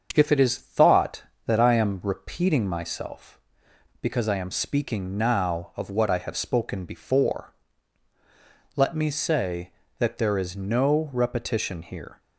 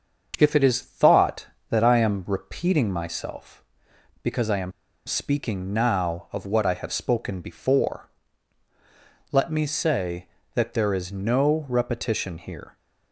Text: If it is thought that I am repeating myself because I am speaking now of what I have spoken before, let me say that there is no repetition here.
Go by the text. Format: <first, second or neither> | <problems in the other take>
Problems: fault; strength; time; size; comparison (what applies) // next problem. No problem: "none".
first | starts louder than the rest; until 1.3 s; 7 dB; also in the first // pauses between "am" and "speaking"; slight; at 4.7 s; 0.35 s long